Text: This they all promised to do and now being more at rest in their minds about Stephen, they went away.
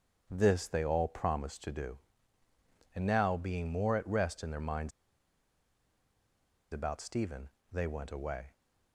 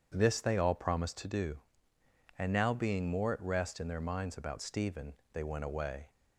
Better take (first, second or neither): second